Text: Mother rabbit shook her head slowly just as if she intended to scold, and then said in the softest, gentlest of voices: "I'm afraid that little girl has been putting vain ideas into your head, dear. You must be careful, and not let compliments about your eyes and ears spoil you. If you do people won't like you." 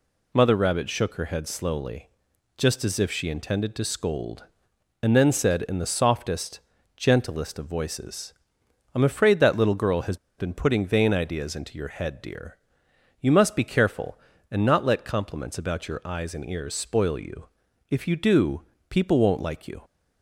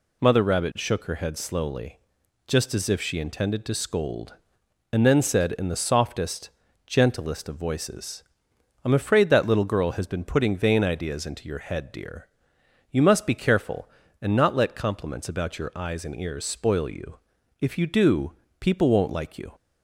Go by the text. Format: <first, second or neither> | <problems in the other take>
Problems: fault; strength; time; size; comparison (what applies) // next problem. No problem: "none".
second | pauses between "slowly" and "just"; noticeable; at 2.0 s; 0.50 s long; noticeable in the second // pauses between "has" and "been"; slight; at 10.1 s; 0.22 s long // pauses between "do" and "people"; slight; at 18.6 s; 0.26 s long; slight in the second